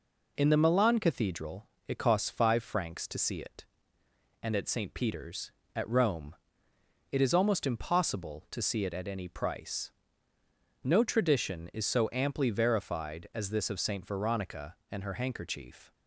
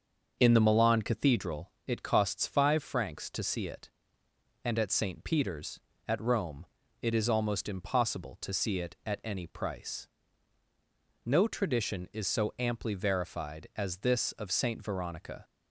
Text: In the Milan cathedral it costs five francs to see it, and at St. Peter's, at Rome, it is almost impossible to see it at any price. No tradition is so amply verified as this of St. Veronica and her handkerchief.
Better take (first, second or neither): first